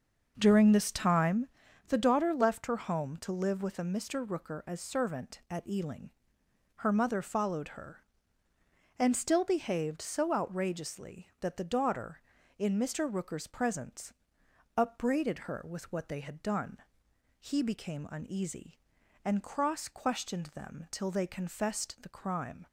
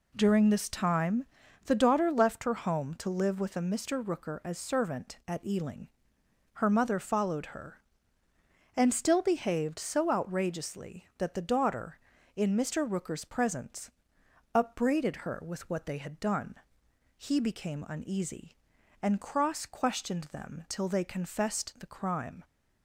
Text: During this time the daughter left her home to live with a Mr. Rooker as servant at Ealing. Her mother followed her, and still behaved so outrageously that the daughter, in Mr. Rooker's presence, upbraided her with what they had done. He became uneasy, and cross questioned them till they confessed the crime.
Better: second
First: starts louder than the rest; noticeable; until 1.4 s; 6 dB // pauses between "time" and "the"; at 1.4 s; 0.40 s long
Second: pauses between "time" and "the"; at 1.2 s; 0.40 s long

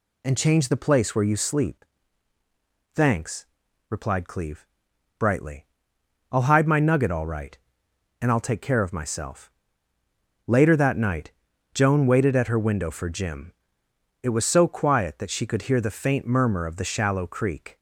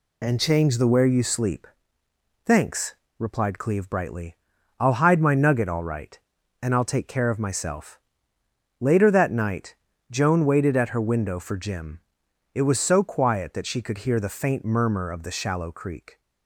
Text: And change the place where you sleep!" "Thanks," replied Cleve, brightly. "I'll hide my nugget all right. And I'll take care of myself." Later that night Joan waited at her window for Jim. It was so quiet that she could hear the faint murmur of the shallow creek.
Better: first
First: pauses between "night" and "Joan"; at 11.3 s; 0.42 s long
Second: skips "place"; at 0.8 s // pauses between "night" and "Joan"; slight; at 9.7 s; 0.36 s long

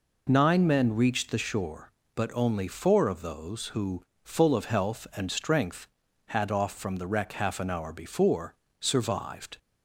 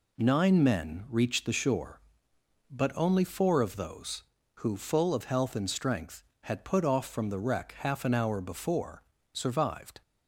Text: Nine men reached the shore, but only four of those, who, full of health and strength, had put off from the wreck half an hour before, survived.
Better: second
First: skips "put"; at 6.5 s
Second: none

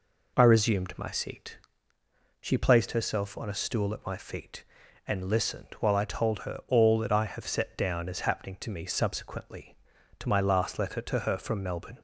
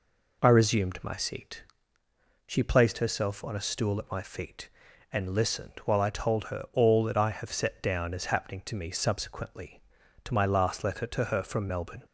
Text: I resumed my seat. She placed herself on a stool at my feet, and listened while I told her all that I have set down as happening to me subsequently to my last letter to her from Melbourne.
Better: neither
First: none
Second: none

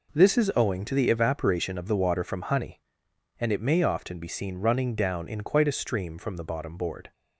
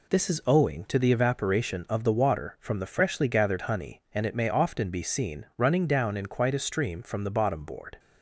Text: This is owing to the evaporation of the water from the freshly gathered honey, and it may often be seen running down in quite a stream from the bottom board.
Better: second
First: skips "the freshly gathered"; at 2.4 s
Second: none

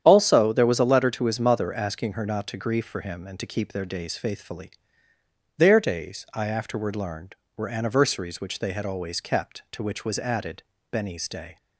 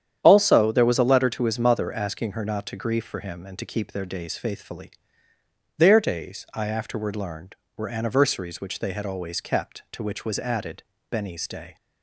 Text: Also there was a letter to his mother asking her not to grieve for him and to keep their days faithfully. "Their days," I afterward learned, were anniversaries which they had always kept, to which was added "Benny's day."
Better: neither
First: starts louder than the rest; strong; until 1.0 s; 9.5 dB // pauses between "added" and "Benny's"; slight; at 10.6 s; 0.30 s long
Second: starts louder than the rest; strong; until 1.2 s; 9.5 dB // pauses between "added" and "Benny's"; slight; at 10.8 s; 0.29 s long

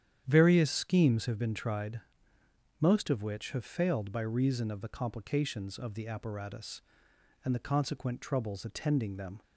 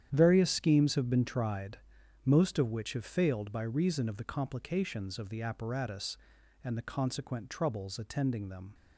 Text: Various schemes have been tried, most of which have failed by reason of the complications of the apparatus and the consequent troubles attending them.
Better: neither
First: starts louder than the rest; strong; until 1.2 s; 9.5 dB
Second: starts louder than the rest; strong; until 1.1 s; 9.5 dB

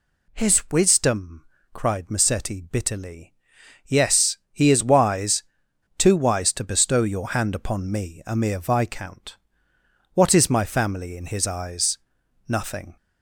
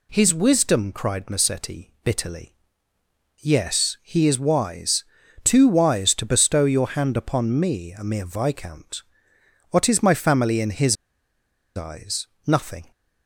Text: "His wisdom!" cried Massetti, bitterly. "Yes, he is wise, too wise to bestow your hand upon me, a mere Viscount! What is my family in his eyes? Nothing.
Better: first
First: none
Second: pauses between "his" and "eyes"; noticeable; at 10.9 s; 0.80 s long

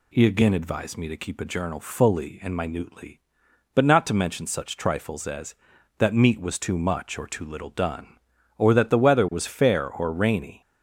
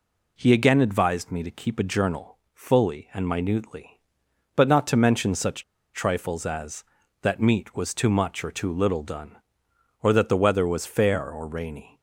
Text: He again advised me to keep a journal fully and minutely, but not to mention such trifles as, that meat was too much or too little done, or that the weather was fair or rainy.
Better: first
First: none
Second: pauses between "journal" and "fully"; slight; at 2.3 s; 0.16 s long // pauses between "such" and "trifles"; slight; at 5.6 s; 0.30 s long

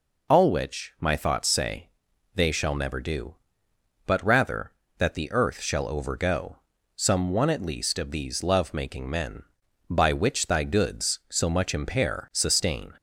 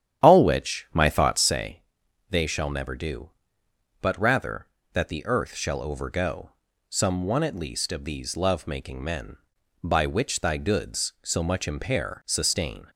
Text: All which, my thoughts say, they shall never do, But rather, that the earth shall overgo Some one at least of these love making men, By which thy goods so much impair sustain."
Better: first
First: pauses between "overgo" and "Some"; at 6.5 s; 0.38 s long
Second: starts louder than the rest; strong; until 1.7 s; 10 dB // pauses between "overgo" and "Some"; at 6.4 s; 0.38 s long

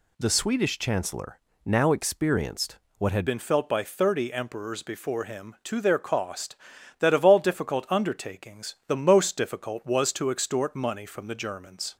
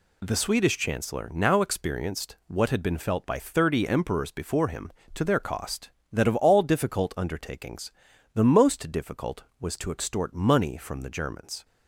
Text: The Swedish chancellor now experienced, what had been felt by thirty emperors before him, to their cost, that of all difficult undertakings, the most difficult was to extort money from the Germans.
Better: second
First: pauses between "chancellor" and "now"; slight; at 1.4 s; 0.24 s long // changes voice at "been"; from 3.2 s on; 8.7 s long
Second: none

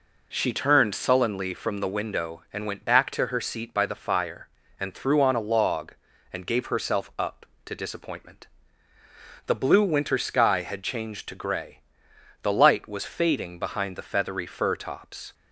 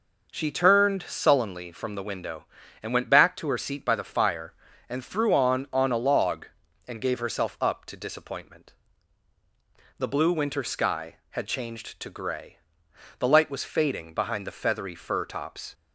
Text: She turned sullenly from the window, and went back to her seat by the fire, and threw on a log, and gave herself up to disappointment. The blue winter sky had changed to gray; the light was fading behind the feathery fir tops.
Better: first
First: none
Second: says "on" twice; at 5.7 s

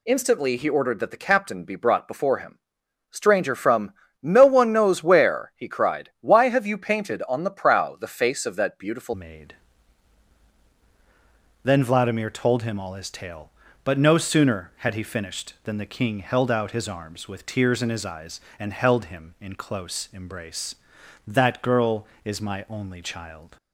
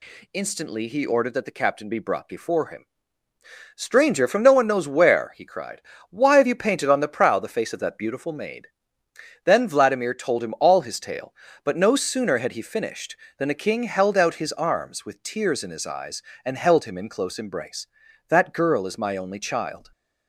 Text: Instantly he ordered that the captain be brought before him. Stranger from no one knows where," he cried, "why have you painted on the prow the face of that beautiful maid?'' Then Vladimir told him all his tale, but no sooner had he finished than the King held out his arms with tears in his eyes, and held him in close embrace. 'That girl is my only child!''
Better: second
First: pauses between "from" and "no"; slight; at 3.9 s; 0.28 s long // changes voice at "maid"; from 9.1 s on; 14.4 s long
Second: none

